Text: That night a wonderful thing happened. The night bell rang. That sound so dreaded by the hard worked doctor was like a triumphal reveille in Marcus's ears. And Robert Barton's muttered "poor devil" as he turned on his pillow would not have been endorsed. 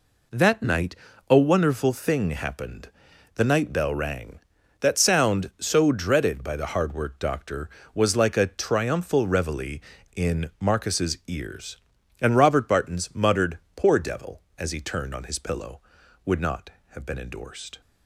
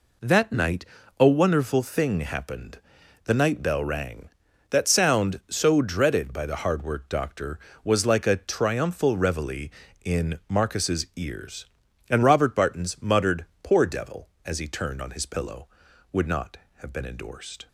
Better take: neither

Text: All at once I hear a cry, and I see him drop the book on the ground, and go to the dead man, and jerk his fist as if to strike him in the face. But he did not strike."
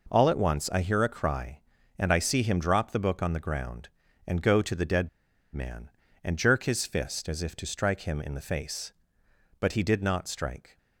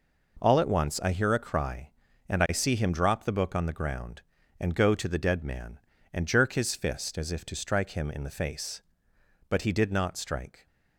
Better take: second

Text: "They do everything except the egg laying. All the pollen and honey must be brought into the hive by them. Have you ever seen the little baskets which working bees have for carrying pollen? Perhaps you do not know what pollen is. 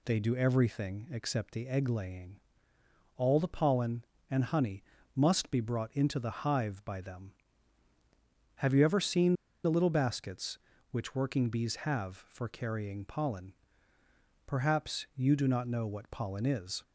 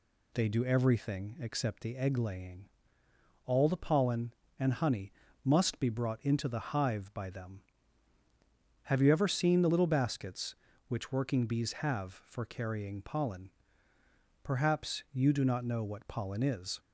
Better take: second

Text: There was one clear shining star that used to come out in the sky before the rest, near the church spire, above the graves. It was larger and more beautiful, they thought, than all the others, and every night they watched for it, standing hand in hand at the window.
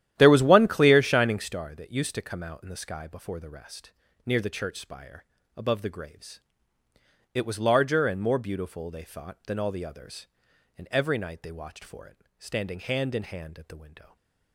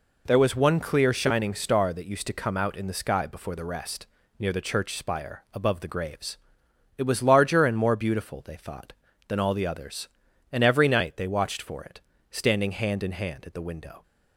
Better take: second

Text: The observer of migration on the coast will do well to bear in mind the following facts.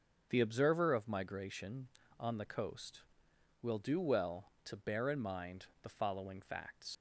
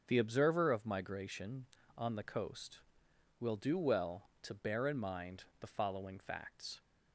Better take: second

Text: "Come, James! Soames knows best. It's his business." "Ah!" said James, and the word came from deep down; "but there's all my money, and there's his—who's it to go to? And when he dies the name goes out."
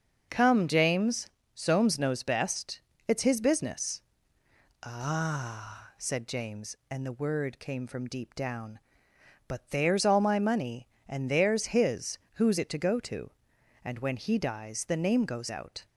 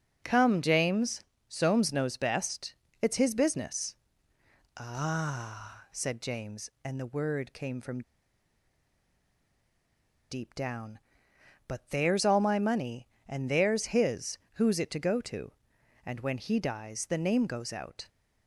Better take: first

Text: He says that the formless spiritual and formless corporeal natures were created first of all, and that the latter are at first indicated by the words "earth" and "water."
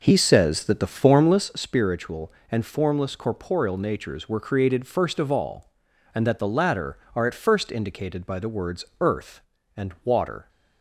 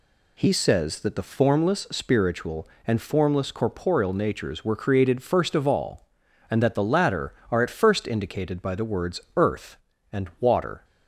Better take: second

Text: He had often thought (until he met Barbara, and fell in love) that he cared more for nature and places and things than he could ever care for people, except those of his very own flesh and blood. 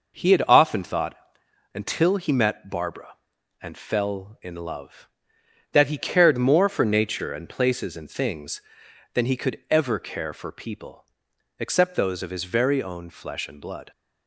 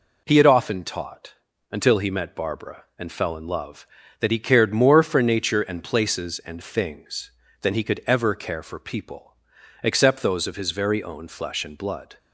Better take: first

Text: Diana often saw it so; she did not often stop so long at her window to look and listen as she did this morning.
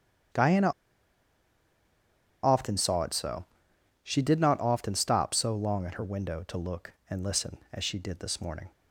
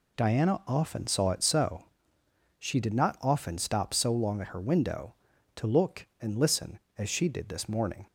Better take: second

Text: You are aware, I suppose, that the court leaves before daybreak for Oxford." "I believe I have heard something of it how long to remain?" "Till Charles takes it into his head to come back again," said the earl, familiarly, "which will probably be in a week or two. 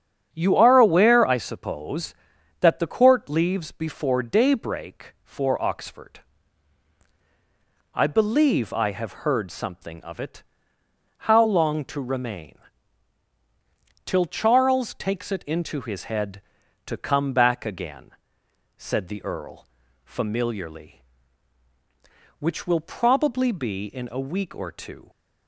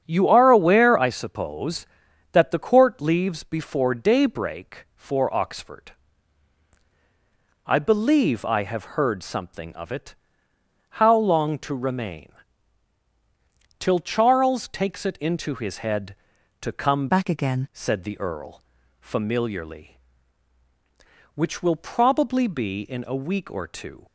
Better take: first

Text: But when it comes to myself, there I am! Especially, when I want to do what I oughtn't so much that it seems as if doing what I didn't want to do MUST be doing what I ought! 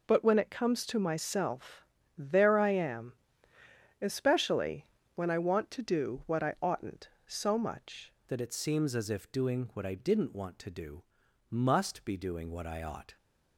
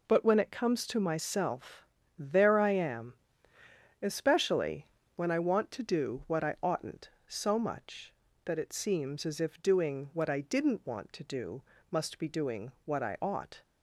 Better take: second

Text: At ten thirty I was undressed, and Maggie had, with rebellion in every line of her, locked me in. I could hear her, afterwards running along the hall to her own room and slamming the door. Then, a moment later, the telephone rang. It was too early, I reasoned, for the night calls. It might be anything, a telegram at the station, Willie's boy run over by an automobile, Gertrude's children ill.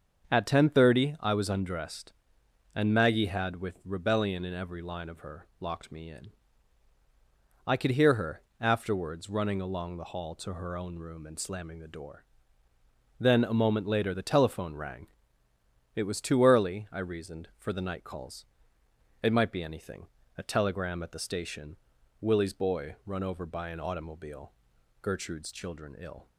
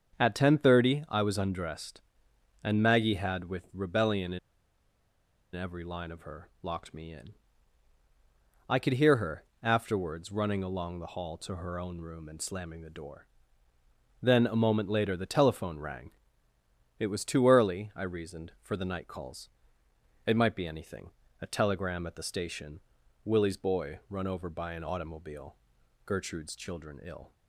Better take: first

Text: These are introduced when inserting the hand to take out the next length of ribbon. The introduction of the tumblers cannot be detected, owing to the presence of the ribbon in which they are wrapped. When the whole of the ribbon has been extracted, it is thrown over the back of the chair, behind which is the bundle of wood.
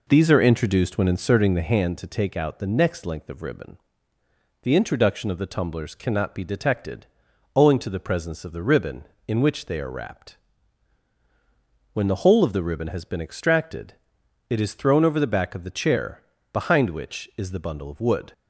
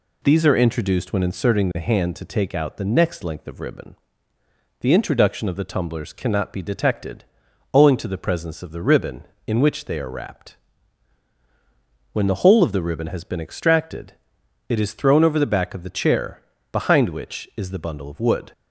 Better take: second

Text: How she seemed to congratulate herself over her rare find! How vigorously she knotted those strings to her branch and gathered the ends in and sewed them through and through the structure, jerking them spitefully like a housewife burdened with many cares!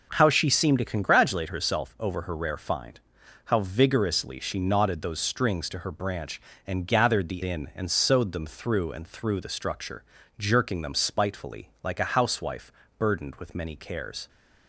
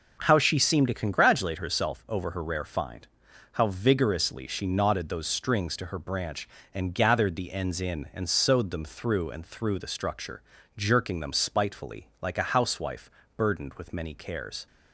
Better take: second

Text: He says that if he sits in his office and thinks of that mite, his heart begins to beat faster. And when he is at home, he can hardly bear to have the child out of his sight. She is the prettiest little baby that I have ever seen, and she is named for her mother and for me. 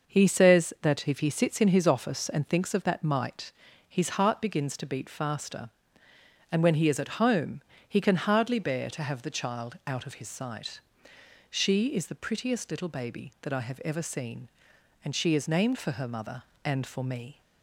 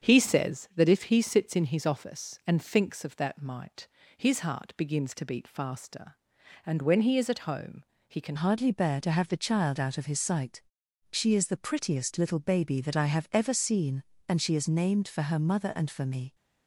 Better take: first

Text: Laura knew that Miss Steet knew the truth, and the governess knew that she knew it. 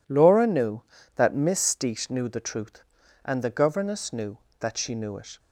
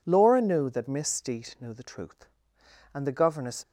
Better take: first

